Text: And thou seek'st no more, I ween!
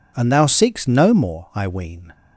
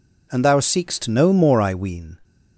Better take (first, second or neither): neither